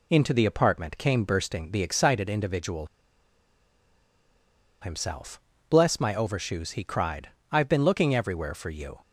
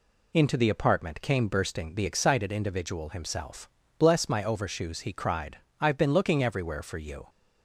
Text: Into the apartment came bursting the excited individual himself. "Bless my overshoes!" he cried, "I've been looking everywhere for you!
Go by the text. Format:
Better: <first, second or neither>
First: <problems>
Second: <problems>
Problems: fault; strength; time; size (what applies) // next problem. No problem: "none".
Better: second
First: pauses between "individual" and "himself"; strong; at 2.8 s; 1.9 s long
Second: none